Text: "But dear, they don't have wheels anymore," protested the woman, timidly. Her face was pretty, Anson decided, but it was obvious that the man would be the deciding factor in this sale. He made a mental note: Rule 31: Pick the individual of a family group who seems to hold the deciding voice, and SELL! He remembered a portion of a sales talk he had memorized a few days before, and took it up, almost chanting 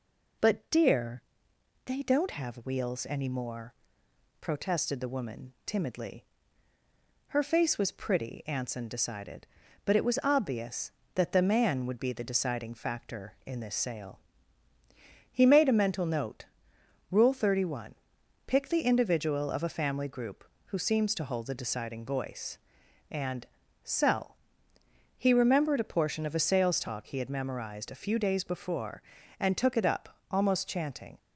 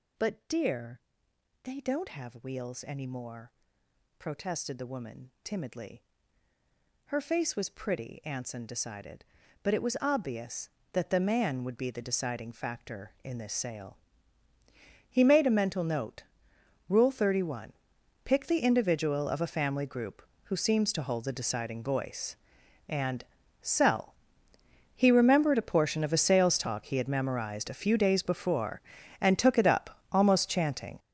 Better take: first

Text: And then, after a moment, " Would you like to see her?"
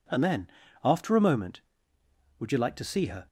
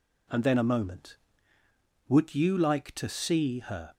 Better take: first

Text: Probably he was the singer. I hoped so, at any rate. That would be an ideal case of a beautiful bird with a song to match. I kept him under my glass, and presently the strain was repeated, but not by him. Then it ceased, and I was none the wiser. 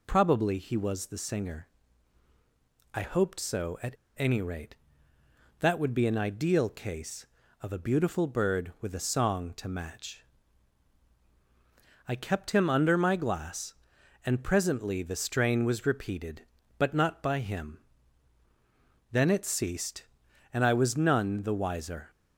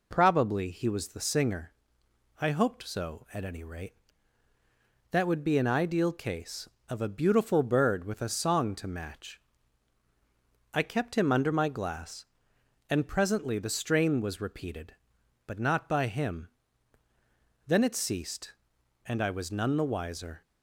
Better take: second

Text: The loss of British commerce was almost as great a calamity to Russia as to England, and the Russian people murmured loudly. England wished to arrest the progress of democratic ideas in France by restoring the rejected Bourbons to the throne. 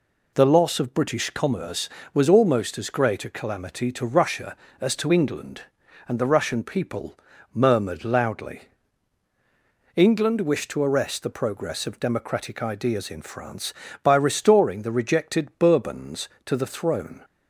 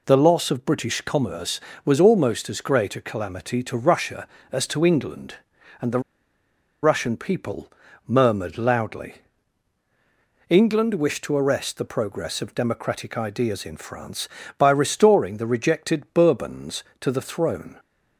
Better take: first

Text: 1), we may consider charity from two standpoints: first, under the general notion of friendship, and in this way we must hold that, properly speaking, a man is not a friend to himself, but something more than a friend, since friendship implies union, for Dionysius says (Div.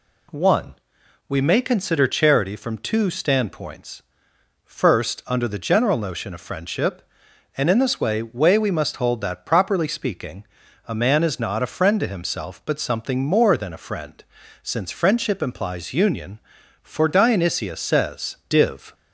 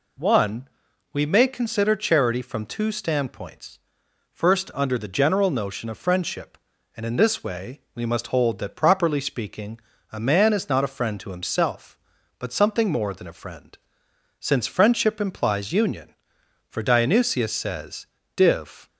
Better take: second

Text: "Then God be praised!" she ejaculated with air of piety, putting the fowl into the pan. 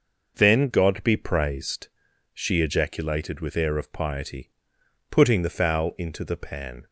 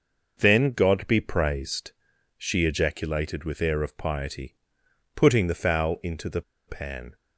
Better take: first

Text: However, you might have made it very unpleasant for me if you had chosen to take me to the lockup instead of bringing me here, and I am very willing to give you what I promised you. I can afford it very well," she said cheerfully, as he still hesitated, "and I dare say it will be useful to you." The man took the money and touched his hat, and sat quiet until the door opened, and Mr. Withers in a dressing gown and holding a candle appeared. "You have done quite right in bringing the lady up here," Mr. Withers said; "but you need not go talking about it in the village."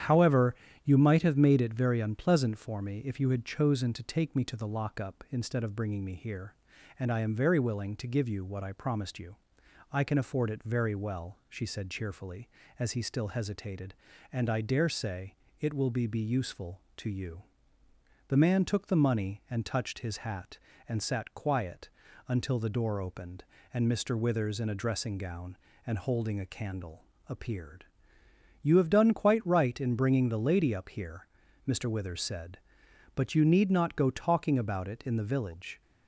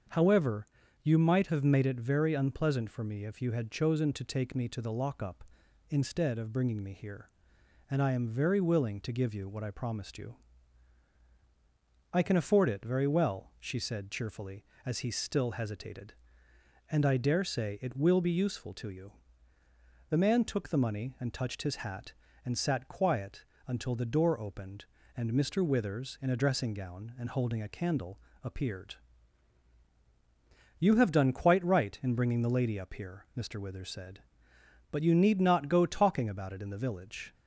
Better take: second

